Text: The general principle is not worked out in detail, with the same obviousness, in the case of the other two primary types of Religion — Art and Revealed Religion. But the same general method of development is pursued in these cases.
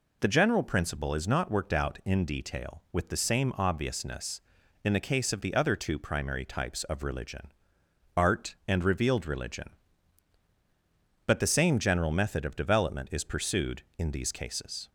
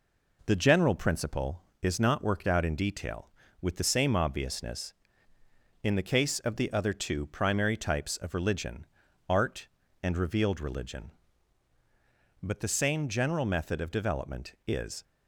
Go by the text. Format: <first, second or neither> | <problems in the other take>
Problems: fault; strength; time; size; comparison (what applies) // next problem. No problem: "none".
first | stops before "pursued in these cases"; at 15.0 s